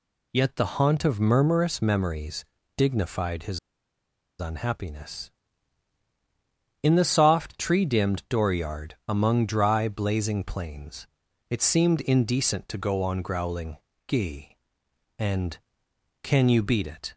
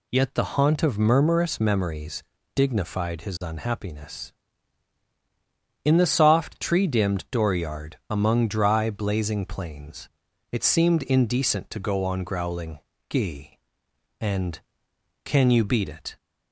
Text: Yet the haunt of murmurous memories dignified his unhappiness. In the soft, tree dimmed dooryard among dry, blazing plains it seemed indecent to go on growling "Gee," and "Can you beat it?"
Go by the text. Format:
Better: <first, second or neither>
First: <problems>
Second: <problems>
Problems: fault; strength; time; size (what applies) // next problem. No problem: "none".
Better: second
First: pauses between "memories" and "dignified"; slight; at 2.4 s; 0.32 s long // pauses between "his" and "unhappiness"; noticeable; at 3.5 s; 0.81 s long // pauses between "dooryard" and "among"; slight; at 8.9 s; 0.16 s long // pauses between "plains" and "it"; at 11.0 s; 0.44 s long // pauses between "growling" and "Gee"; slight; at 13.7 s; 0.30 s long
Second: pauses between "memories" and "dignified"; slight; at 2.2 s; 0.32 s long // pauses between "dooryard" and "among"; slight; at 7.9 s; 0.16 s long // pauses between "plains" and "it"; at 10.0 s; 0.44 s long // pauses between "growling" and "Gee"; slight; at 12.7 s; 0.30 s long